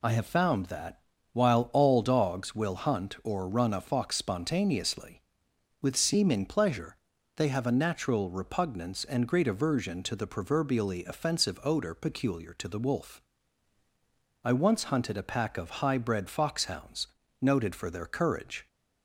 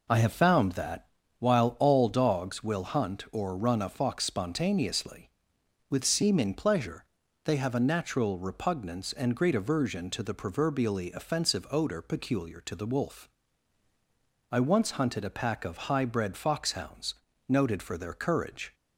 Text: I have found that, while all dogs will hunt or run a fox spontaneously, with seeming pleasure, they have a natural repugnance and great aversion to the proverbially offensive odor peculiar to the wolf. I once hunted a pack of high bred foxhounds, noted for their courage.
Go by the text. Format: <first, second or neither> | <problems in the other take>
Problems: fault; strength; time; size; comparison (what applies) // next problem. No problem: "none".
first | starts louder than the rest; noticeable; until 1.1 s; 4 dB